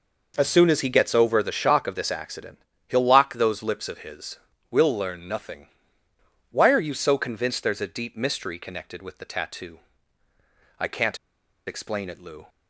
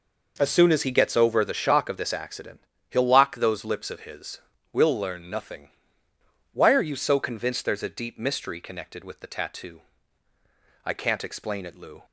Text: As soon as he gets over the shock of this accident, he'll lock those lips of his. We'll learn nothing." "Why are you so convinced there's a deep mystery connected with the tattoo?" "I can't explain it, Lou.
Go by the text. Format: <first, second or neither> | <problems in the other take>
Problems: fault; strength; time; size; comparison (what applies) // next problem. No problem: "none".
second | pauses between "can't" and "explain"; noticeable; at 11.1 s; 0.49 s long